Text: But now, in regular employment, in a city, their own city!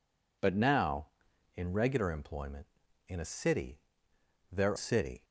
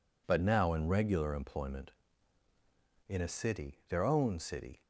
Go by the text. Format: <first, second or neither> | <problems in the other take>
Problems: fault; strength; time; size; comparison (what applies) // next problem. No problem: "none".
second | skips "own"; at 4.7 s